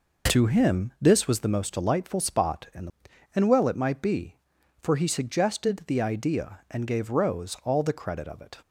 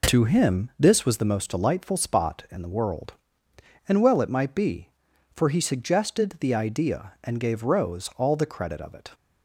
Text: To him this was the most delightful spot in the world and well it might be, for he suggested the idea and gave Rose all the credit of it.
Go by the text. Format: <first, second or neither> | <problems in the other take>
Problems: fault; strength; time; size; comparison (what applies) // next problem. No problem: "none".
second | skips "world"; at 3.1 s